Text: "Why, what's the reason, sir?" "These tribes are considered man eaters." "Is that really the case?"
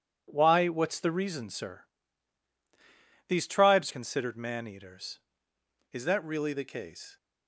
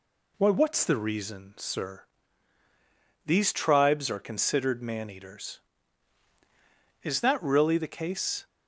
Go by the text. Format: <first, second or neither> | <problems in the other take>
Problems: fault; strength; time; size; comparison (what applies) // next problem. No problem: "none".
second | skips "are"; at 3.9 s